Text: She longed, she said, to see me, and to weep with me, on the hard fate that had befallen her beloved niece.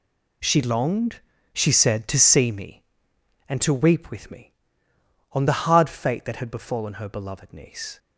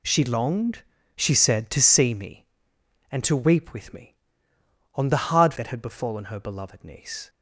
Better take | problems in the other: first | skips "fate"; at 5.5 s

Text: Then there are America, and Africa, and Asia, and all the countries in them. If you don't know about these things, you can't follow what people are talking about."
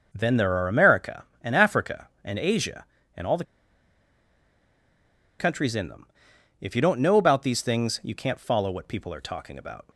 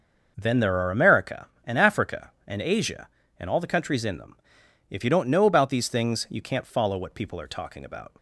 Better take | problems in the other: second | starts louder than the rest; noticeable; until 1.1 s; 6 dB // pauses between "the" and "countries"; strong; at 3.4 s; 1.9 s long

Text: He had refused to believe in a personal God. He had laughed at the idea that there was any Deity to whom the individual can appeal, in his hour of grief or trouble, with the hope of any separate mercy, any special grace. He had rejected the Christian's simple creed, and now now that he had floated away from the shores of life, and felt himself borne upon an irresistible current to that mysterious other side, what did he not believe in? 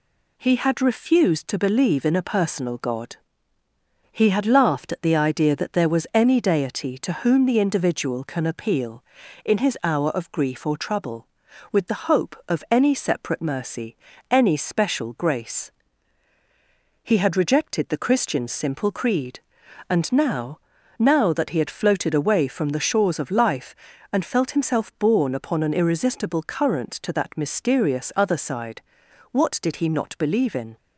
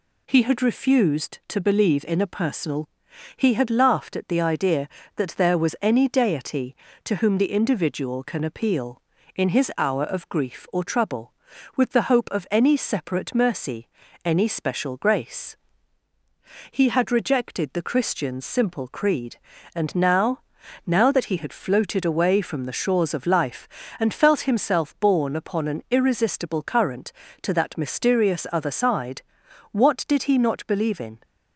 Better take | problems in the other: first | skips "God"; at 3.0 s // pauses between "now" and "now"; noticeable; at 20.3 s; 0.46 s long; also in the first

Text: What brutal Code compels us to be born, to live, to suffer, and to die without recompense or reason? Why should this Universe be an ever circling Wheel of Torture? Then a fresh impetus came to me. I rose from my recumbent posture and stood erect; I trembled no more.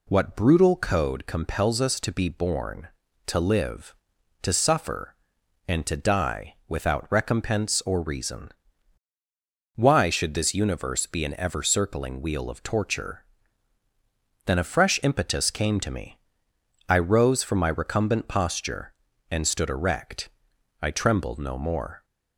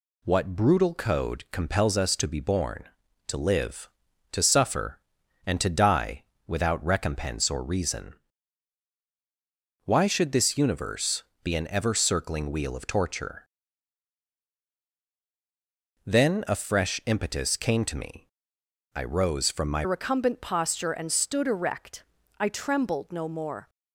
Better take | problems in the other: first | pauses between "die" and "without"; slight; at 6.2 s; 0.24 s long // pauses between "Universe" and "be"; slight; at 11.2 s; 0.18 s long // changes voice at "recumbent"; from 19.8 s on; 3.8 s long

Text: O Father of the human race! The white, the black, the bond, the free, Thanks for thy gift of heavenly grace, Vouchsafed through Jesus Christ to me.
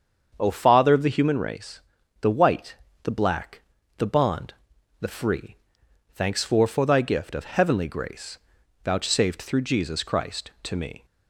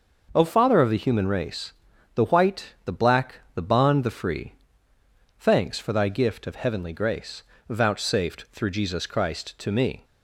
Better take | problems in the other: second | starts louder than the rest; strong; until 1.4 s; 7 dB // says "for" twice; at 6.6 s

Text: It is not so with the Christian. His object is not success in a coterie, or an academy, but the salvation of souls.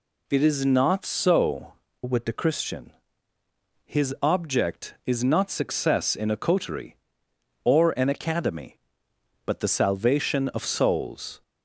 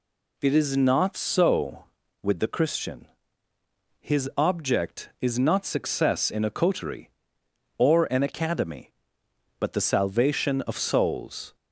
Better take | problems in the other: second | changes voice from "with" to "the"; from 2.0 to 2.3 s; 0.3 s long

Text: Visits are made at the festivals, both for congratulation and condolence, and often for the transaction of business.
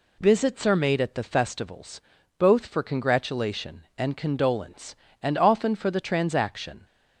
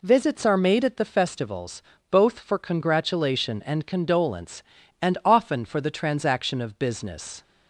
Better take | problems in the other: second | stops before "of business"; at 6.8 s

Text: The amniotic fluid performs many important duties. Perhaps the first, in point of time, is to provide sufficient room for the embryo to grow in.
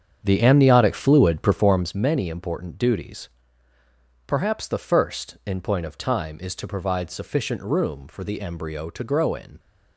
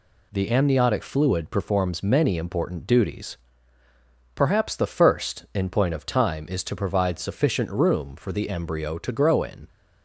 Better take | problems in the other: second | starts louder than the rest; strong; until 2.0 s; 7.5 dB

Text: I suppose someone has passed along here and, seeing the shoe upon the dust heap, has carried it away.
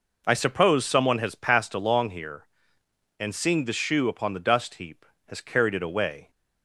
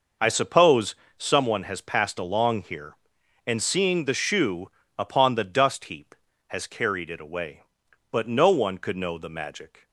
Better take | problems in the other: first | pauses between "suppose" and "someone"; slight; at 0.9 s; 0.22 s long // pauses between "shoe" and "upon"; slight; at 4.7 s; 0.26 s long // goes on to say "But no one could know the magic"; strong; from 8.1 s on; 1.7 s long

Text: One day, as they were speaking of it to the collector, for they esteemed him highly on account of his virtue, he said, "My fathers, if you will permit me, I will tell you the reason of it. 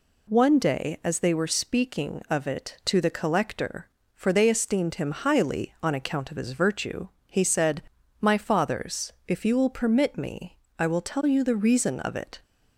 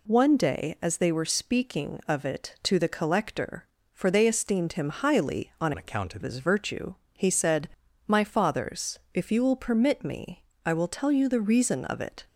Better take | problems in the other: first | changes voice from "account" to "of"; from 5.7 to 6.2 s; 0.5 s long

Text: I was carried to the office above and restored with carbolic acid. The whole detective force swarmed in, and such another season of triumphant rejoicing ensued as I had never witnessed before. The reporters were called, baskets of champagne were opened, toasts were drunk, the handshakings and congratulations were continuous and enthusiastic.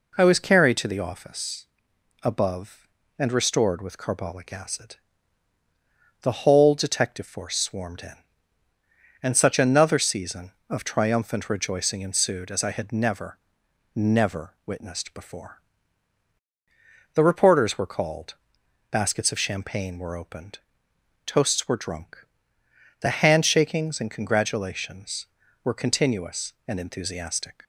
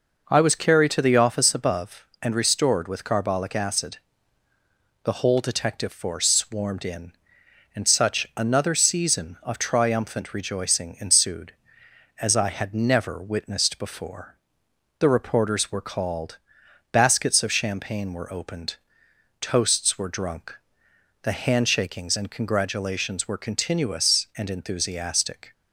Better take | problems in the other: second | pauses between "office" and "above"; noticeable; at 1.6 s; 0.56 s long // says "never" twice; at 13.9 s

